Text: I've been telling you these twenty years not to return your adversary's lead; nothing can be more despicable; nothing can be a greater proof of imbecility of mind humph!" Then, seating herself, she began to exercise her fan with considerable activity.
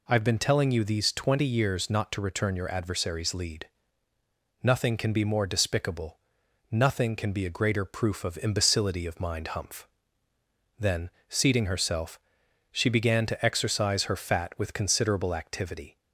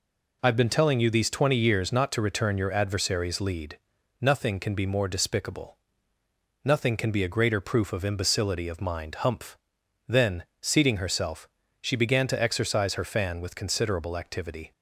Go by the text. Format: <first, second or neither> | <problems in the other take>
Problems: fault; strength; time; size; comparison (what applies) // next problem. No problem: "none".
second | says "fat" for "fan"; at 14.1 s